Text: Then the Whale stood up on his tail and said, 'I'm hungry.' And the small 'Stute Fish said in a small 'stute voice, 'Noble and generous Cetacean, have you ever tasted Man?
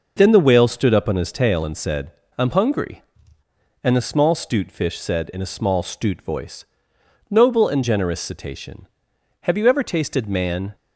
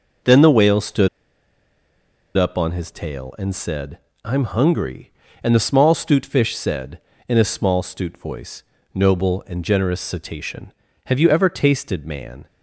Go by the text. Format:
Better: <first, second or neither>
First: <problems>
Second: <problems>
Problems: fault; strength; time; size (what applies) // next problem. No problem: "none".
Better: first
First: none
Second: pauses between "stood" and "up"; strong; at 1.0 s; 1.2 s long